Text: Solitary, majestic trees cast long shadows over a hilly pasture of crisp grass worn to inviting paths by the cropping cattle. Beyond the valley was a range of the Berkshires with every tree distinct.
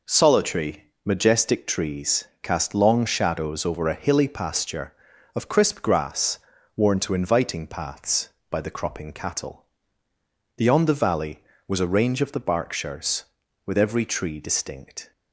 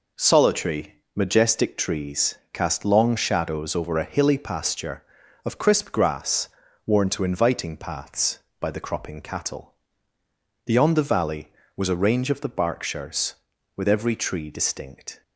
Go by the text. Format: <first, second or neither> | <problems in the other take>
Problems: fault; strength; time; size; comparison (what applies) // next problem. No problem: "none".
neither | pauses between "trees" and "cast"; slight; the same in both // pauses between "grass" and "worn"; slight; the same in both